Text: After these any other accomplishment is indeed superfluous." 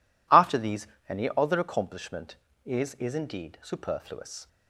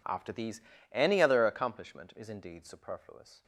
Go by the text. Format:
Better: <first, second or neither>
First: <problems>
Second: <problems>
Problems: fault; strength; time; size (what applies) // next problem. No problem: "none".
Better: second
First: pauses between "these" and "any"; slight; at 0.8 s; 0.22 s long // says "is" twice; at 2.9 s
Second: pauses between "these" and "any"; slight; at 0.6 s; 0.30 s long